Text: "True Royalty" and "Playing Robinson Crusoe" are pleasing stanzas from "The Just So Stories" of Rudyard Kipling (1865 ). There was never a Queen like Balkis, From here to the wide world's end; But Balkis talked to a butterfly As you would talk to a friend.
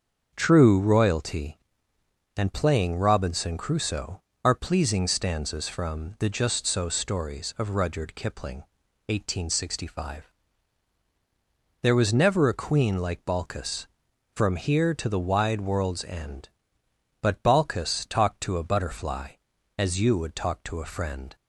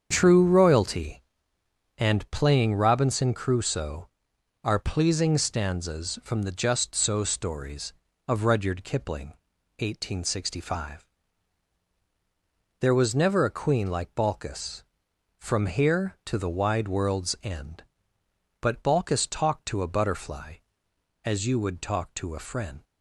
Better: neither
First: starts louder than the rest; until 1.3 s; 6.5 dB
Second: starts louder than the rest; strong; until 1.1 s; 7.5 dB

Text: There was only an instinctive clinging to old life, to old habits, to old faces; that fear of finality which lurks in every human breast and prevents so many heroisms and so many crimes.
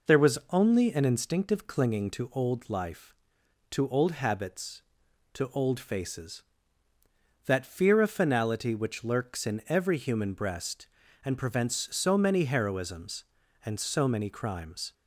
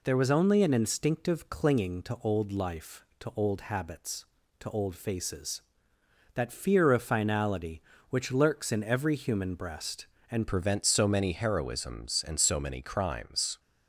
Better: first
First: none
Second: changes voice at "prevents"; from 10.4 s on; 3.1 s long

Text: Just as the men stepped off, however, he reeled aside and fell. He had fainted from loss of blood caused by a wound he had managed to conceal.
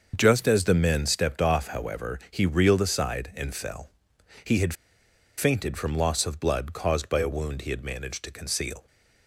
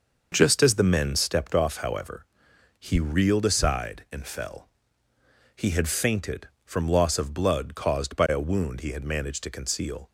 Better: second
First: starts louder than the rest; until 1.1 s; 6.5 dB // pauses between "had" and "fainted"; noticeable; at 4.7 s; 0.63 s long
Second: starts louder than the rest; noticeable; until 1.3 s; 6 dB

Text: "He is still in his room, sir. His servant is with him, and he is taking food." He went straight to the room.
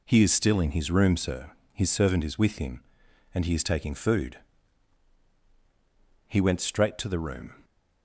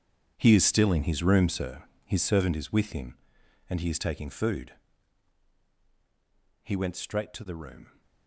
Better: first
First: none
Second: gets quieter; strong; throughout; 15.5 dB

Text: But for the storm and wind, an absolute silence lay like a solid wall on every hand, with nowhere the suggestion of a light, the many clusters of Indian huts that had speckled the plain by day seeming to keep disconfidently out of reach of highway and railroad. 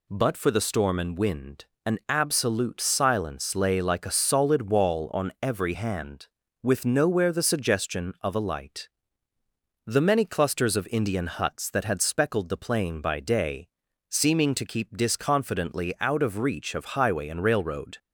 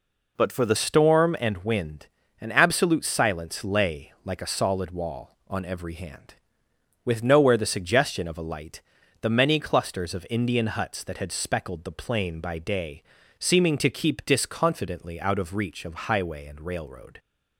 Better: first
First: pauses between "day" and "seeming"; at 13.6 s; 0.40 s long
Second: changes voice at "storm"; from 0.7 s on; 16.4 s long // pauses between "day" and "seeming"; at 13.0 s; 0.40 s long

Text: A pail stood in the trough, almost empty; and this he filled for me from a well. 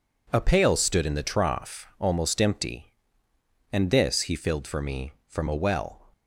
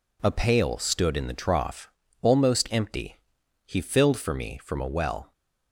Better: first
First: none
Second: skips "and this"; at 3.4 s

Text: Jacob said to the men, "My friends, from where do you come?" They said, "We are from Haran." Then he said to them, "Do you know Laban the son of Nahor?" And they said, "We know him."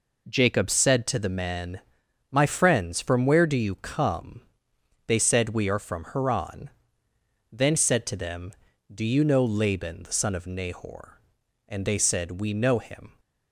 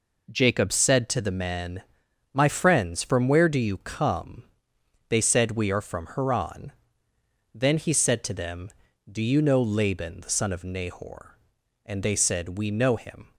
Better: second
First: skips "he"; at 7.7 s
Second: none

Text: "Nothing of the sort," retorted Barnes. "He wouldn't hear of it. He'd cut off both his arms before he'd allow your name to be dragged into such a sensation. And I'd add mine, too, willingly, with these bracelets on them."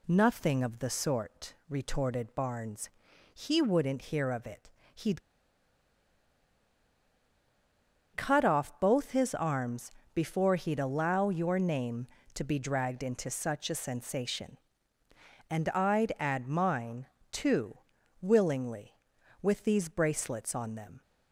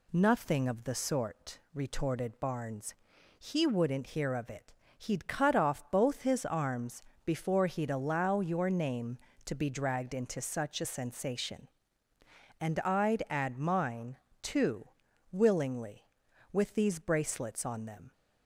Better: second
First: pauses between "He'd" and "cut"; strong; at 5.2 s; 2.9 s long // pauses between "arms" and "before"; slight; at 9.9 s; 0.24 s long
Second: pauses between "arms" and "before"; slight; at 7.0 s; 0.24 s long

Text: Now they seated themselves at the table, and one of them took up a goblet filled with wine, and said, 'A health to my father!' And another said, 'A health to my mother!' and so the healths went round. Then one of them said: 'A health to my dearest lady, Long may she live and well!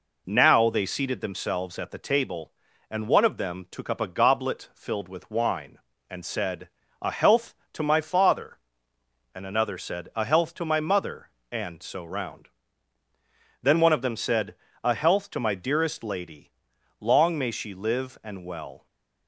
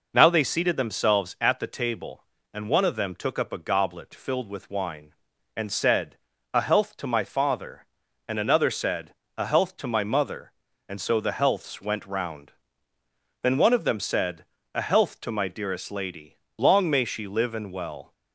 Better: second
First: skips "the healths went"; at 12.0 s // stays silent after the last word; slight; from 18.7 s on; 0.5 s long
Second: none

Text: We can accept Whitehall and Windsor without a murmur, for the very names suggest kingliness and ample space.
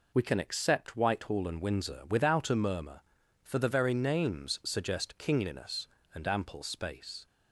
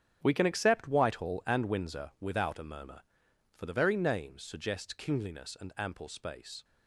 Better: first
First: none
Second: gets quieter; strong; throughout; 12.5 dB

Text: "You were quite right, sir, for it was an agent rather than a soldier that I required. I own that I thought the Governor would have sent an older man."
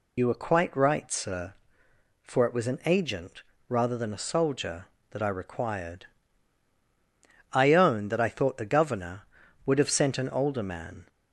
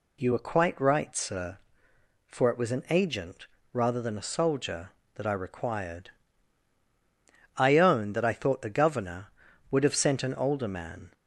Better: second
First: loses the start of "You"; at 0.1 s; 50 ms // pauses between "agent" and "rather"; slight; at 3.4 s; 0.26 s long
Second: pauses between "agent" and "rather"; slight; at 3.4 s; 0.26 s long

